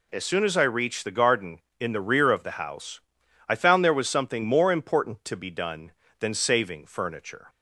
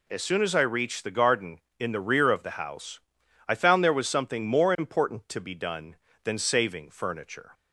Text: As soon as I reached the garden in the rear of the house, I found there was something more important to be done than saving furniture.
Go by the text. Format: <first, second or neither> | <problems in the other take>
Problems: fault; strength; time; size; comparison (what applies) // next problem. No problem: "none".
neither | none